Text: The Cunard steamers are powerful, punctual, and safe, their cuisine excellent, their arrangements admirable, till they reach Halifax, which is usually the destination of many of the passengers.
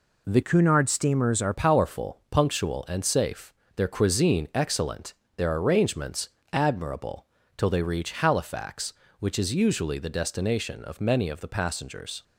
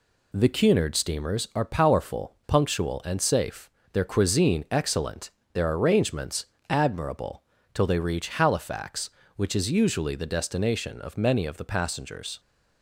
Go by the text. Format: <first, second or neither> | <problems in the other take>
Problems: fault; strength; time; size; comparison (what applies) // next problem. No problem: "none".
second | changes voice from "Cunard" to "are"; from 0.4 to 1.5 s; 1.1 s long // pauses between "arrangements" and "admirable"; slight; at 6.2 s; 0.22 s long; slight in the second